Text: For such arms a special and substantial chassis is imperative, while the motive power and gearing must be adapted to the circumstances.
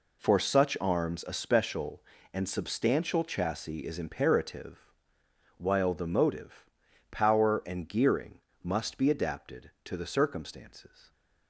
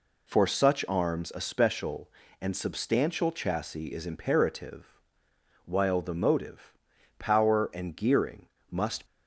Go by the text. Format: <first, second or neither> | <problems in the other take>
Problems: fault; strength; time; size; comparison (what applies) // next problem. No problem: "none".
first | pauses between "motive" and "power"; at 6.7 s; 0.44 s long; also in the first // pauses between "gearing" and "must"; slight; at 8.4 s; 0.22 s long; slight in the first // stops before "be adapted to the circumstances"; at 9.0 s